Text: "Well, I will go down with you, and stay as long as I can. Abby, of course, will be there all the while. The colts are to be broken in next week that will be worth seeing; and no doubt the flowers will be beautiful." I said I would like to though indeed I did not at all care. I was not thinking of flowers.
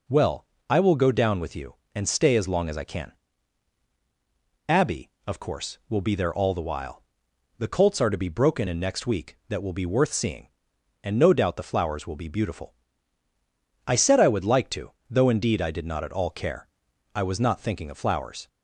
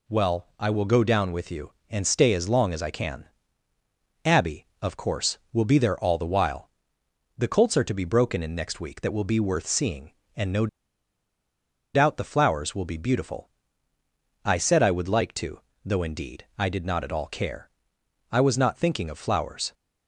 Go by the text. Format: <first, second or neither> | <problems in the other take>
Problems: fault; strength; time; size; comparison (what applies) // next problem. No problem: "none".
first | pauses between "no" and "doubt"; strong; at 10.6 s; 1.2 s long // pauses between "to" and "though"; slight; at 15.5 s; 0.24 s long; slight in the first